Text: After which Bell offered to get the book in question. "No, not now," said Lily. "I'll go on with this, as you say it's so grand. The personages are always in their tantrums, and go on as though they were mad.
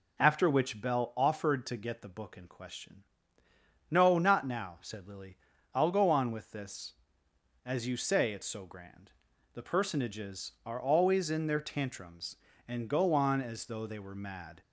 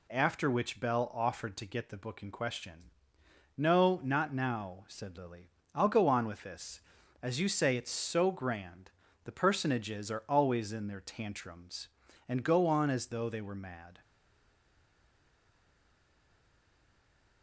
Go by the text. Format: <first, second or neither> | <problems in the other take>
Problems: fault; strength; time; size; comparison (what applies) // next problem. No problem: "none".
first | stays silent after the last word; strong; from 14.0 s on; 3.4 s long